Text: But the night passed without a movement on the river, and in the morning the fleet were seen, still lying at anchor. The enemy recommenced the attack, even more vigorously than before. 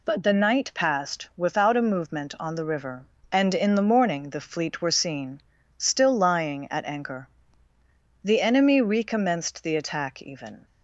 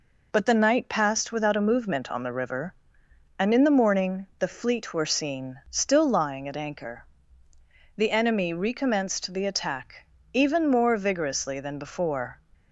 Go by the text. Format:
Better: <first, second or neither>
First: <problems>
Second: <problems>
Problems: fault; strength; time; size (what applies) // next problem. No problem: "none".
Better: second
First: stops before "more vigorously than before"; at 10.6 s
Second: none